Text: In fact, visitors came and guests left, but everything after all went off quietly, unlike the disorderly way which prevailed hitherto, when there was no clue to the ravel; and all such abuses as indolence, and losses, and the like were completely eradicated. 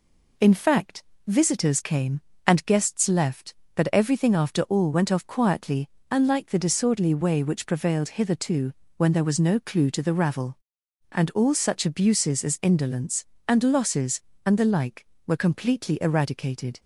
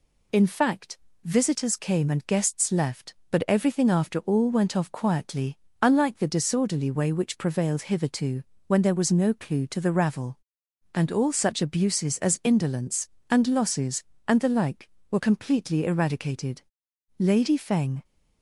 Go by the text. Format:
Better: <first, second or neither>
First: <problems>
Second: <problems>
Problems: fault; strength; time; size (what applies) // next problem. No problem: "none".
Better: first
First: none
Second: goes on to say "Lady Feng"; noticeable; from 17.1 s on; 0.86 s long